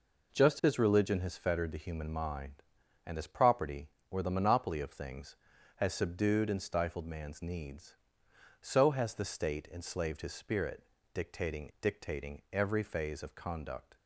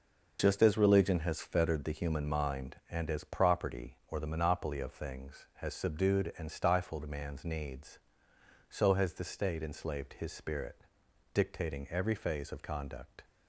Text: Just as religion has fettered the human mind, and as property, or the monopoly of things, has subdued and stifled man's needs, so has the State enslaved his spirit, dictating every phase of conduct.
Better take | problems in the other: second | says "dictating" twice; at 11.8 s

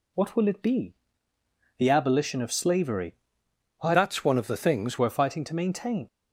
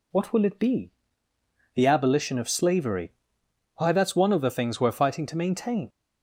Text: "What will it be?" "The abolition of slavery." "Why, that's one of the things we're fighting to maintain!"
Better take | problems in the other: second | changes voice from "that's" to "things"; from 3.9 to 4.9 s; 1.0 s long

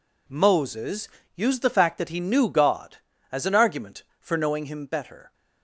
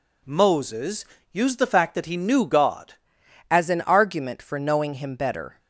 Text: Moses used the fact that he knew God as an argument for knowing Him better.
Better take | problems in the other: first | pauses between "Moses" and "used"; slight; at 1.0 s; 0.28 s long; slight in the first // changes voice at "as"; from 3.4 s on; 2.1 s long

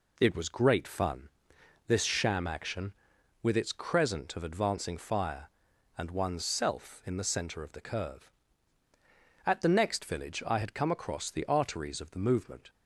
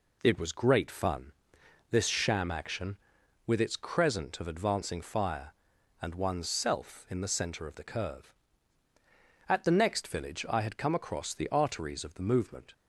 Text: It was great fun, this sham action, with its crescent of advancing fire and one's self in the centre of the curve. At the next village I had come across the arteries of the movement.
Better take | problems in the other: neither | none

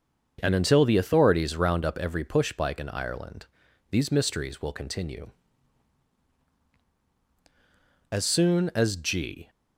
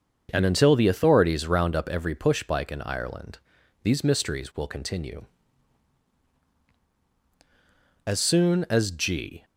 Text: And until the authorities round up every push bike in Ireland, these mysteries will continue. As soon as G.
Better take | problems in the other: neither | starts louder than the rest; the same in both

